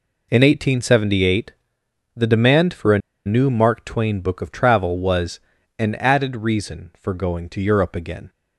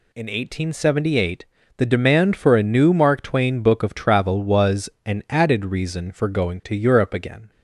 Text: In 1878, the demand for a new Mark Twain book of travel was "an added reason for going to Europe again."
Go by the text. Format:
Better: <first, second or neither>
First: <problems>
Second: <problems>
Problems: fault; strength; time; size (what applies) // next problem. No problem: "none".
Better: second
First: pauses between "a" and "new"; slight; at 2.9 s; 0.27 s long // pauses between "was" and "an"; at 5.3 s; 0.40 s long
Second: pauses between "was" and "an"; slight; at 4.9 s; 0.16 s long